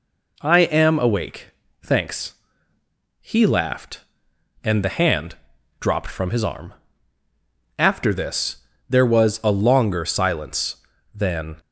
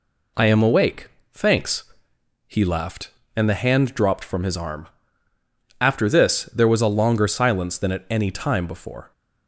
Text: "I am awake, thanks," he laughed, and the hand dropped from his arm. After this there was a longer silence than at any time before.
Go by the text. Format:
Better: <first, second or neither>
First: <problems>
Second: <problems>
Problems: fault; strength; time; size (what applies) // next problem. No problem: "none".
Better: second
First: pauses between "hand" and "dropped"; at 5.3 s; 0.44 s long // pauses between "this" and "there"; slight; at 8.5 s; 0.32 s long // stops before "at any time before"; at 11.5 s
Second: none